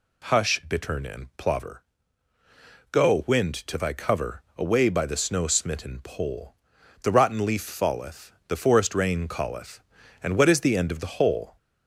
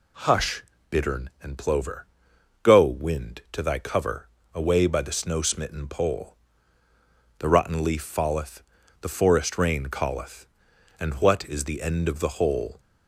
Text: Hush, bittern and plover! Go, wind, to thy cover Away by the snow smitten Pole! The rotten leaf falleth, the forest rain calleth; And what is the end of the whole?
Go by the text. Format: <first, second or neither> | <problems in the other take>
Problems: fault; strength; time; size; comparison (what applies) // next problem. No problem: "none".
second | gets louder; throughout; 3.5 dB // pauses between "cover" and "Away"; slight; at 4.4 s; 0.16 s long; slight in the second